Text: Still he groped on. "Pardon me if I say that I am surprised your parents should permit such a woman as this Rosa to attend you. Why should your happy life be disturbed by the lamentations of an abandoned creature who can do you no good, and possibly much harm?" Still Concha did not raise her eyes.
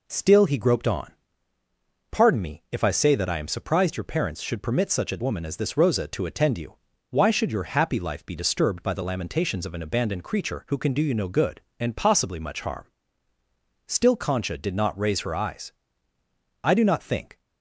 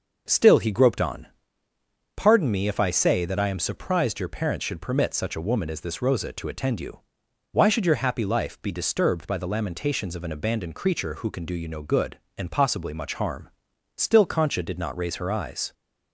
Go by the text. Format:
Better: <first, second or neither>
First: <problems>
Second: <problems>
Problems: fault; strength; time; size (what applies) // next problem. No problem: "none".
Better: second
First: goes on to say "I do not think"; noticeable; from 16.6 s on; 0.78 s long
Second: none